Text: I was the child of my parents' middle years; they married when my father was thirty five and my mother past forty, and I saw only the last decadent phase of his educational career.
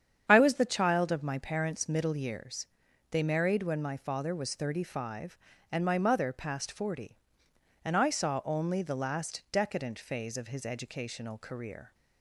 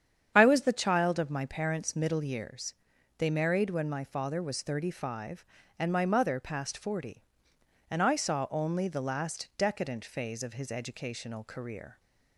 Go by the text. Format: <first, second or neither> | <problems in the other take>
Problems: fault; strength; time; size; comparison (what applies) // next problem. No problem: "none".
neither | starts louder than the rest; strong; the same in both